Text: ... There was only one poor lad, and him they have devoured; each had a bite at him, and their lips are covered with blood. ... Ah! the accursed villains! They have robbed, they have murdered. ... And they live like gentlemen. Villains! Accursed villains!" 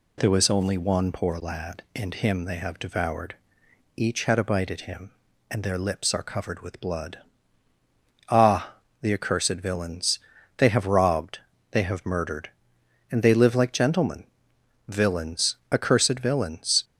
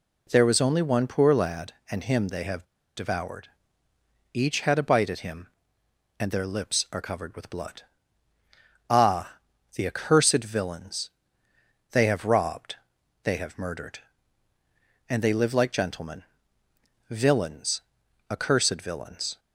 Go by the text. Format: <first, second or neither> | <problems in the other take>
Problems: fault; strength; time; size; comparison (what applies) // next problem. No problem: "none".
first | pauses between "have" and "devoured"; slight; at 2.6 s; 0.32 s long